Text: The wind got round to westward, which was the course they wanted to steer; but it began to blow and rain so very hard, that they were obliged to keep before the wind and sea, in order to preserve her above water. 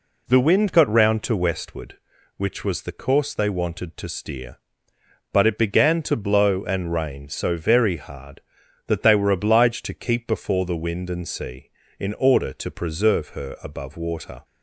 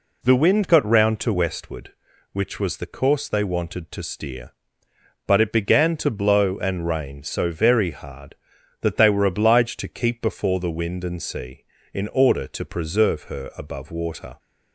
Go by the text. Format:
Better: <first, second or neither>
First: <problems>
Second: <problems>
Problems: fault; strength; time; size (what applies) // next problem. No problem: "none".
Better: neither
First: none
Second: none